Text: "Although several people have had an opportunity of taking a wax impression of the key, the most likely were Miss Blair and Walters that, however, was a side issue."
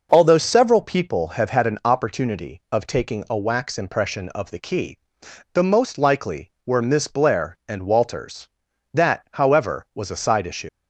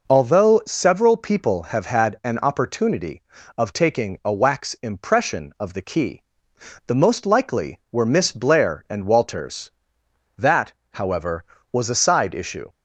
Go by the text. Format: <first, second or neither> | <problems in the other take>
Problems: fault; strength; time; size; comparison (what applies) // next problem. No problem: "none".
second | leaves "issue" unfinished; at 10.6 s; 90 ms